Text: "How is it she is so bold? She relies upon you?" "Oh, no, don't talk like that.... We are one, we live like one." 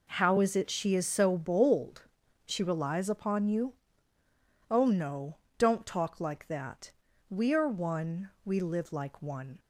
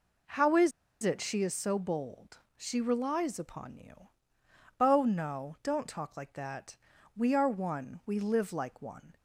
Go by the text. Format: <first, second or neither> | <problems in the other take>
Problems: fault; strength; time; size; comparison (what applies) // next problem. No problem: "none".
first | pauses between "is" and "it"; slight; at 0.7 s; 0.32 s long